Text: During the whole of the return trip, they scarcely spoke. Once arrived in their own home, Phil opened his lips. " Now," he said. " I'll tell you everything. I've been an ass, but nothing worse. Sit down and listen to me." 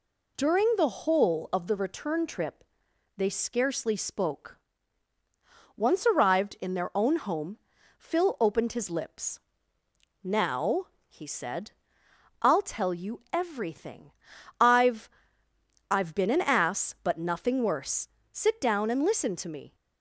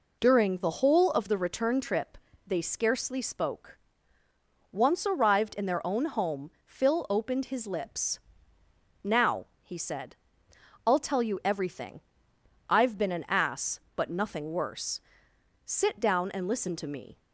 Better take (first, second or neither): second